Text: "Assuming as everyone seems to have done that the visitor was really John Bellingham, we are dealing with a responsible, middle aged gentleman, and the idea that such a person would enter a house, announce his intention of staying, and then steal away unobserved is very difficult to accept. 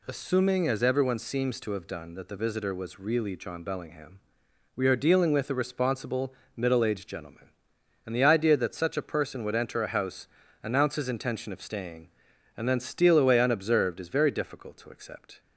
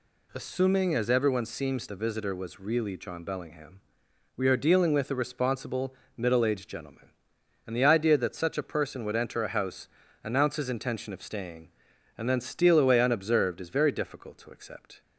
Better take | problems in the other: first | skips "to have done that"; at 1.8 s

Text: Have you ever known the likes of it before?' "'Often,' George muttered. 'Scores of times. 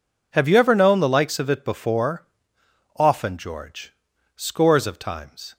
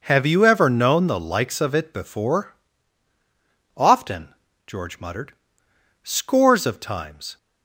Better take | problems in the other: second | skips "muttered"; at 4.1 s

